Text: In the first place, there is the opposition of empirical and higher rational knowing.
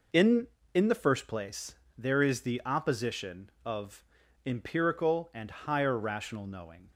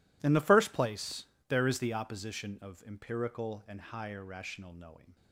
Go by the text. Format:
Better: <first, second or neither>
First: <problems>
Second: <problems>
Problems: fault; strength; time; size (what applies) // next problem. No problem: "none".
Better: second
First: says "In" twice; at 0.7 s // pauses between "of" and "empirical"; at 4.0 s; 0.40 s long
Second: none